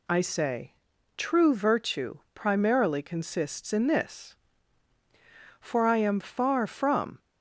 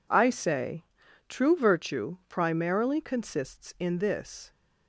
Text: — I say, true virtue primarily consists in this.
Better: second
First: goes on to say "For I am far from"; from 5.5 s on; 1.6 s long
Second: none

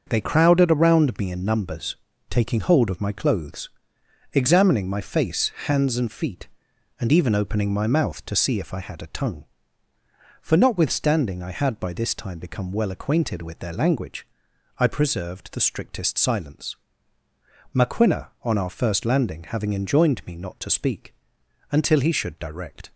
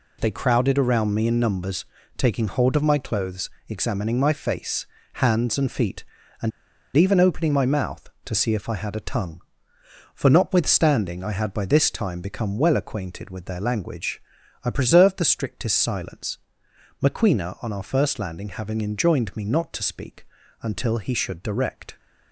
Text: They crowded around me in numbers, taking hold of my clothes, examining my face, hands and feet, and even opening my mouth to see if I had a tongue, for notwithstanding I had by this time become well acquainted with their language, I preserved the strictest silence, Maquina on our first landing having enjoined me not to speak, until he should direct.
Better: first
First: none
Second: pauses between "and" and "even"; noticeable; at 6.5 s; 0.46 s long

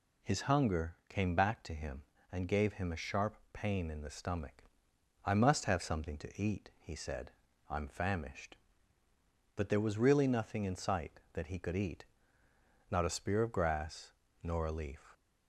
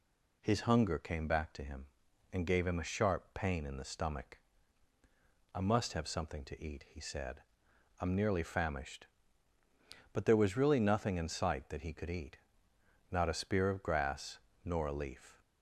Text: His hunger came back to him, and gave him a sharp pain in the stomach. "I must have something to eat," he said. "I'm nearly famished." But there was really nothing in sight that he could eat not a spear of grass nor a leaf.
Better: second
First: pauses between "sharp" and "pain"; slight; at 3.3 s; 0.16 s long // skips "nearly"; at 7.8 s // pauses between "eat" and "not"; noticeable; at 12.0 s; 0.84 s long // pauses between "grass" and "nor"; slight; at 14.1 s; 0.28 s long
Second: pauses between "eat" and "not"; noticeable; at 12.3 s; 0.74 s long // pauses between "grass" and "nor"; slight; at 14.3 s; 0.26 s long

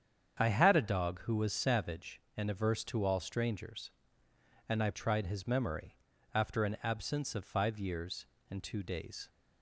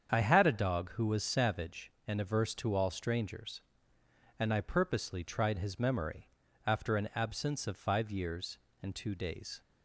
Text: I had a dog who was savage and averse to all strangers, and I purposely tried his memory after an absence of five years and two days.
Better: second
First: starts louder than the rest; strong; until 1.4 s; 8 dB // skips "purposely"; at 4.9 s // pauses between "memory" and "after"; at 5.9 s; 0.38 s long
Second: starts louder than the rest; strong; until 1.1 s; 7.5 dB // pauses between "memory" and "after"; at 6.2 s; 0.38 s long

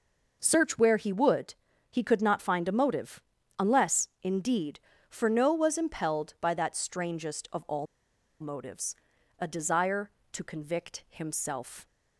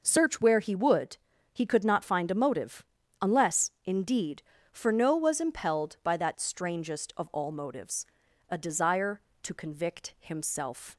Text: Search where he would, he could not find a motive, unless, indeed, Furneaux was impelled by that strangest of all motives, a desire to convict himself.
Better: second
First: pauses between "all" and "motives"; noticeable; at 7.8 s; 0.55 s long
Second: none

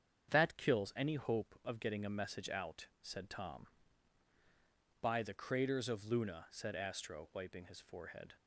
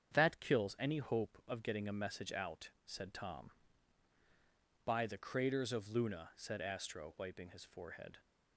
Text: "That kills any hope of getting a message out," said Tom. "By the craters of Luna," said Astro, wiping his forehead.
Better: neither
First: starts louder than the rest; strong; until 1.3 s; 8 dB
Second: starts louder than the rest; strong; until 1.1 s; 8 dB

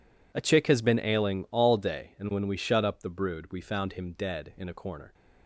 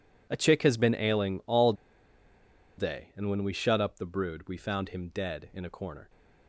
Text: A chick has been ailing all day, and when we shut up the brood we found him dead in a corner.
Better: first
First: none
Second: pauses between "all" and "day"; at 1.7 s; 1.0 s long

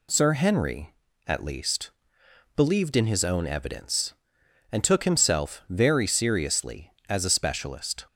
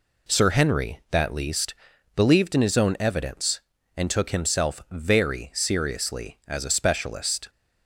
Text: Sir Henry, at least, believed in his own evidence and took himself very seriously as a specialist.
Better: first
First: none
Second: says "that" for "at"; at 1.1 s

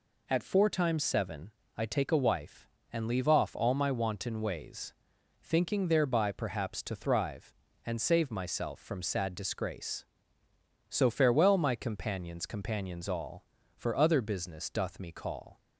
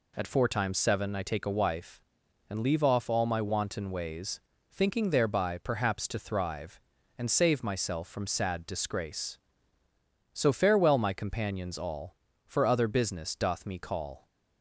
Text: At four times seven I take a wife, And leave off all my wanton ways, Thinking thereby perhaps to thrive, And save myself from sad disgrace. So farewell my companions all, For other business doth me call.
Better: second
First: pauses between "seven" and "I"; slight; at 1.5 s; 0.24 s long // says "companions" twice; at 12.4 s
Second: none

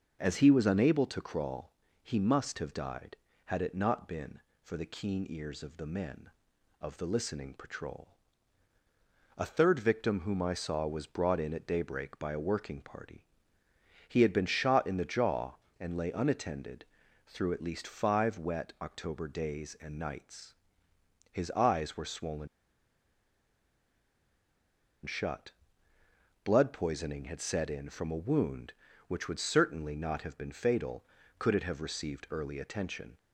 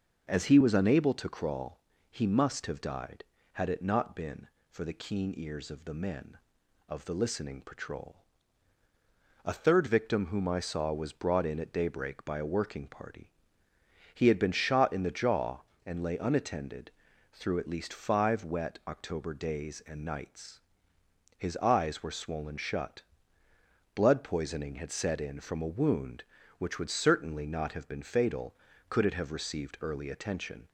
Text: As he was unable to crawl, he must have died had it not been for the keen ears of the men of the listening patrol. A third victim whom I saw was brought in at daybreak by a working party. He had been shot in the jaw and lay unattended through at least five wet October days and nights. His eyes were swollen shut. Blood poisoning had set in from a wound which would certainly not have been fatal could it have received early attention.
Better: second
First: pauses between "unattended" and "through"; at 16.8 s; 0.42 s long // pauses between "swollen" and "shut"; strong; at 22.4 s; 2.5 s long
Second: pauses between "unattended" and "through"; at 16.8 s; 0.42 s long

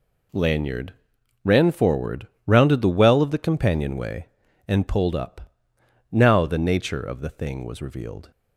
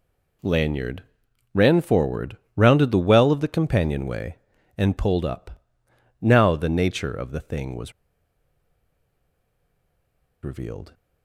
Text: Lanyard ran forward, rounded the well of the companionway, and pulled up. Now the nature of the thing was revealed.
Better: first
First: pauses between "Lanyard" and "ran"; noticeable; at 0.9 s; 0.50 s long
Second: pauses between "Lanyard" and "ran"; noticeable; at 1.0 s; 0.50 s long // pauses between "was" and "revealed"; strong; at 7.9 s; 2.5 s long

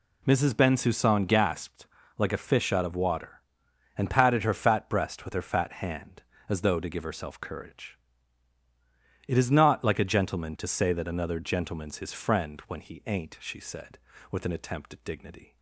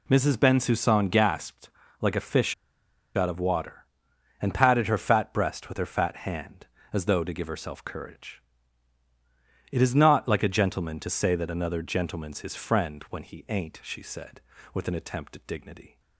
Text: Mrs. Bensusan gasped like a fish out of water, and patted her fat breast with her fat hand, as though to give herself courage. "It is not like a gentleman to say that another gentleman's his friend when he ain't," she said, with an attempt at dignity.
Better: first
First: pauses between "gasped" and "like"; slight; at 1.8 s; 0.30 s long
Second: pauses between "gasped" and "like"; slight; at 1.6 s; 0.30 s long // pauses between "fish" and "out"; noticeable; at 2.5 s; 0.61 s long

